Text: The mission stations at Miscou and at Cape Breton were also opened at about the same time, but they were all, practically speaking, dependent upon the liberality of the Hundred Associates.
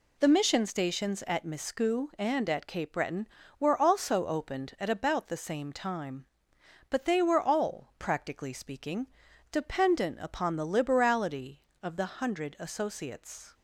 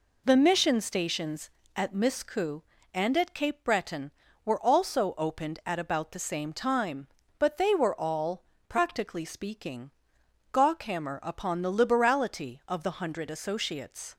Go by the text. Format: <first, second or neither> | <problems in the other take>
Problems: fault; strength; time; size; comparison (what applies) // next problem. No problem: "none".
first | says "gawkhammer" for "dependent"; at 10.5 s